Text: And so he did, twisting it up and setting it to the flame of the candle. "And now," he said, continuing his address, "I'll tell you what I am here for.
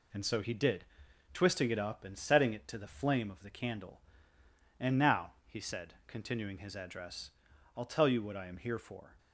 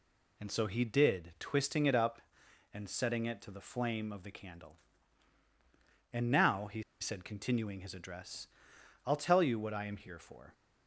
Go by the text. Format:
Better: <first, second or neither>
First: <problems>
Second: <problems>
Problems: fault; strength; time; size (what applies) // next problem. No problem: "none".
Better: first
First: none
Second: pauses between "he" and "said"; slight; at 6.8 s; 0.17 s long